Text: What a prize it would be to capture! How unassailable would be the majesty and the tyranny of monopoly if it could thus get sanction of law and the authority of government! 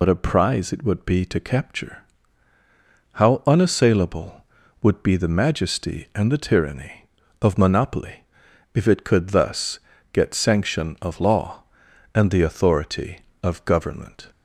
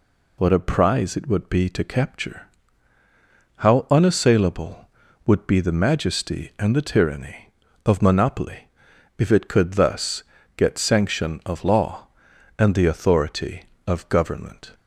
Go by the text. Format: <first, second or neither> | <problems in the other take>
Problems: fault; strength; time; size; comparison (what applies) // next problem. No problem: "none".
second | loses the start of "What"; at 0.0 s; 60 ms // pauses between "monopoly" and "if"; noticeable; at 8.2 s; 0.48 s long; noticeable in the second // pauses between "thus" and "get"; slight; at 9.7 s; 0.32 s long; slight in the second